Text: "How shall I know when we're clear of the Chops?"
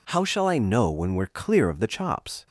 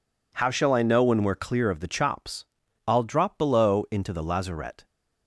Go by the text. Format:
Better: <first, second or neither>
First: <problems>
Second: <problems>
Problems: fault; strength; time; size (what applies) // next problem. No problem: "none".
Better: first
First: none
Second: goes on to say "I'll drop below into the lazarette"; strong; from 2.8 s on; 1.9 s long